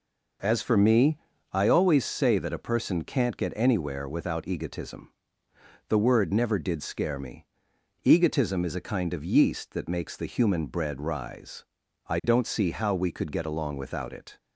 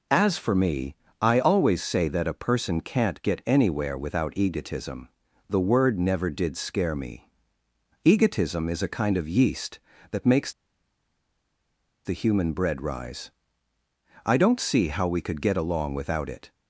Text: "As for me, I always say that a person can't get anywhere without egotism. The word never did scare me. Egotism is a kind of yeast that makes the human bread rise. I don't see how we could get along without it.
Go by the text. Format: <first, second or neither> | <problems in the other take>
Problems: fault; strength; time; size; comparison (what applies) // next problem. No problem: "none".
first | pauses between "makes" and "the"; strong; at 10.5 s; 1.5 s long